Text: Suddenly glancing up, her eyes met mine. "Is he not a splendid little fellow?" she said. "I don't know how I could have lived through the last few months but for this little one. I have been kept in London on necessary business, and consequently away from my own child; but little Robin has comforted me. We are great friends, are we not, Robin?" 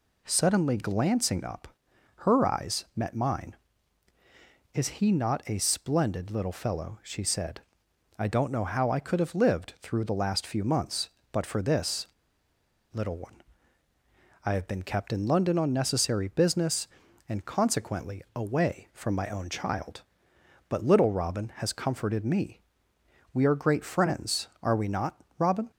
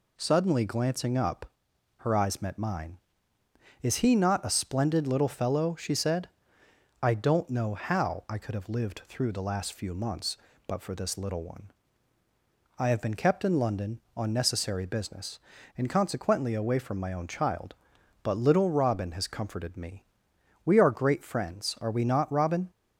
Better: second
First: pauses between "this" and "little"; noticeable; at 12.0 s; 0.87 s long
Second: none

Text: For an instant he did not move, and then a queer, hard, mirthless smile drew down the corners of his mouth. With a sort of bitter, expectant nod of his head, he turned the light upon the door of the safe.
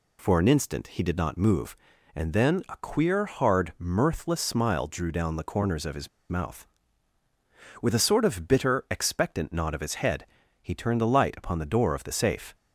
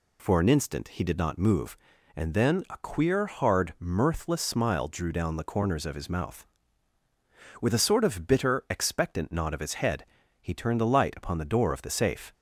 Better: second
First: pauses between "his" and "mouth"; slight; at 6.0 s; 0.22 s long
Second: none

